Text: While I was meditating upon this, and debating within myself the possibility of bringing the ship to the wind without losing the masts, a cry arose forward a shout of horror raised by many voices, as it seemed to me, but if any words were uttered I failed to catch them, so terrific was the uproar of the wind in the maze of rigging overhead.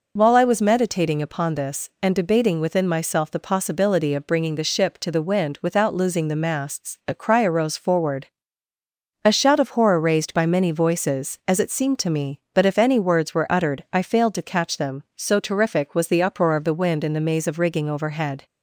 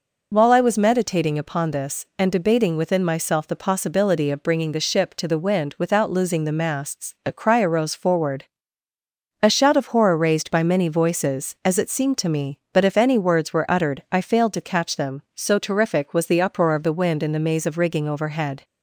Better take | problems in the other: neither | pauses between "forward" and "a"; noticeable; the same in both

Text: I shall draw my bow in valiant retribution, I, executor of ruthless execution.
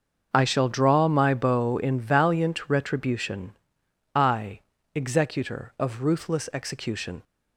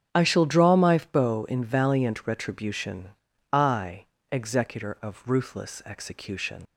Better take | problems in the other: first | starts louder than the rest; strong; until 1.2 s; 11 dB; also in the first // leaves "execution" unfinished; at 6.6 s; 60 ms

